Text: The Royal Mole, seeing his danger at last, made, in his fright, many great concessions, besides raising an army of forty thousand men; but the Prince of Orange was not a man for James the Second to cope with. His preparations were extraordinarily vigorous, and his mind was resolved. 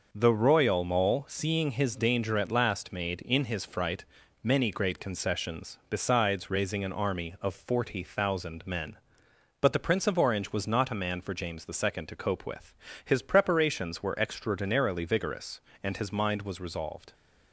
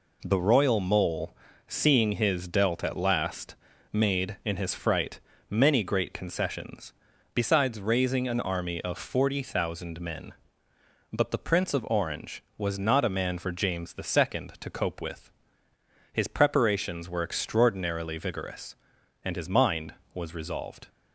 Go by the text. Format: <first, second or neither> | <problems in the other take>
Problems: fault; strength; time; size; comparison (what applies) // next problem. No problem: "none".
first | says "dealt" for "danger"; at 2.4 s